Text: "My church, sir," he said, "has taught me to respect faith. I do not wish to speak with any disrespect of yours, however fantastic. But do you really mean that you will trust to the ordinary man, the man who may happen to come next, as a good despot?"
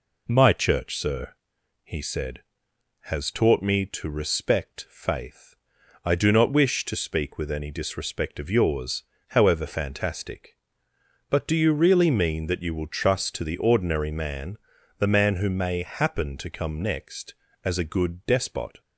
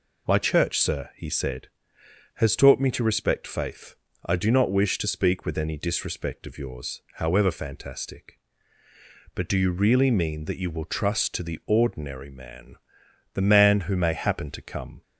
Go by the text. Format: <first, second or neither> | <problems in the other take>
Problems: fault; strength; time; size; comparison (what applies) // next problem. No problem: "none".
first | stops before "next as a good despot"; at 15.0 s